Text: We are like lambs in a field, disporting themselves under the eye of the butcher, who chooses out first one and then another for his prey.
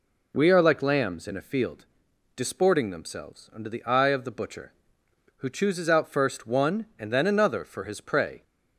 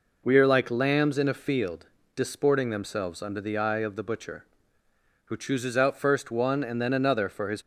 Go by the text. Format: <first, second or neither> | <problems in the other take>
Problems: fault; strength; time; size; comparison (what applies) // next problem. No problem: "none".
first | stops before "prey"; at 7.6 s